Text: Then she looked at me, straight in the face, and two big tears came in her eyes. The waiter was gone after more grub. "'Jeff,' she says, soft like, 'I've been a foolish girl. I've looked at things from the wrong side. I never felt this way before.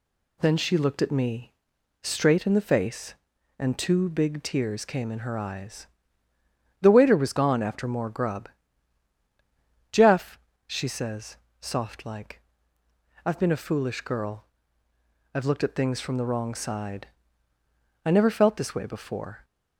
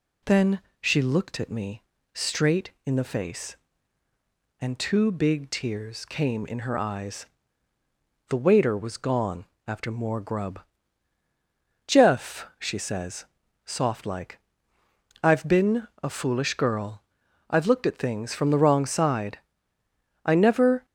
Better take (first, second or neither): first